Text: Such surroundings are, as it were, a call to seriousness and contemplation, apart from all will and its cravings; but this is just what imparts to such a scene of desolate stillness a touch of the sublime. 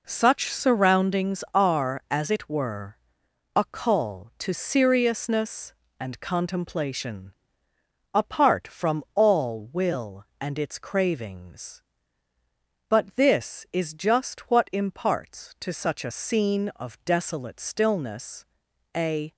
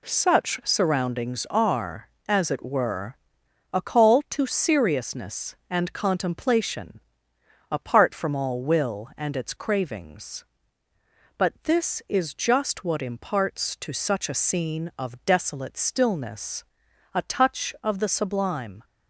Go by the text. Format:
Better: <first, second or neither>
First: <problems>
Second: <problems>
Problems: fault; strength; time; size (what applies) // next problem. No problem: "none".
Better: second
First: pauses between "stillness" and "a"; noticeable; at 18.4 s; 0.50 s long // stops before "touch of the sublime"; at 19.3 s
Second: pauses between "stillness" and "a"; noticeable; at 16.6 s; 0.50 s long